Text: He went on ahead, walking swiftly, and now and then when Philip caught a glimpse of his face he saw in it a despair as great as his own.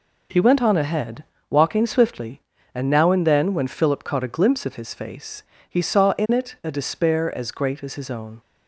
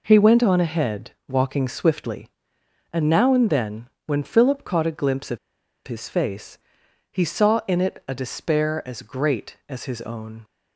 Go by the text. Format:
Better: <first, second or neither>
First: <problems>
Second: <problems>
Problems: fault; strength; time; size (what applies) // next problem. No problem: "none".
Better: first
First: pauses between "face" and "he"; slight; at 5.4 s; 0.26 s long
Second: pauses between "then" and "when"; slight; at 3.8 s; 0.18 s long // pauses between "of" and "his"; noticeable; at 5.3 s; 0.48 s long // pauses between "face" and "he"; noticeable; at 6.5 s; 0.52 s long